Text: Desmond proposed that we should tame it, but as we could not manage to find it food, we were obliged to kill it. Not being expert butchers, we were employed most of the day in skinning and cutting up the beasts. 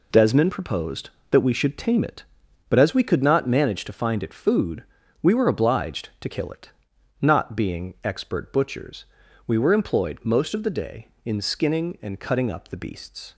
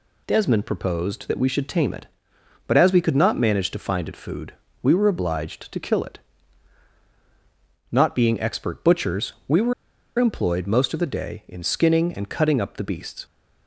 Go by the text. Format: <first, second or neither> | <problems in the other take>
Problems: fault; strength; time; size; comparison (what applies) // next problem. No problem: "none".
first | pauses between "were" and "employed"; noticeable; at 9.7 s; 0.45 s long